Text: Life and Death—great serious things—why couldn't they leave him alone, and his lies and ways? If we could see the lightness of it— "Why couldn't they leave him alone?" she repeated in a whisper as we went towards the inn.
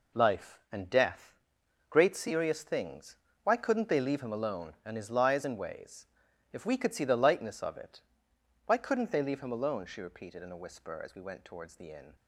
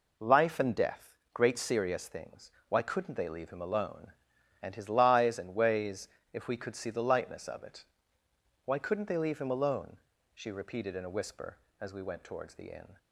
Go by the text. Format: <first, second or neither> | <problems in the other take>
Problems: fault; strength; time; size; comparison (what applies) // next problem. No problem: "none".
second | gets quieter; strong; throughout; 9 dB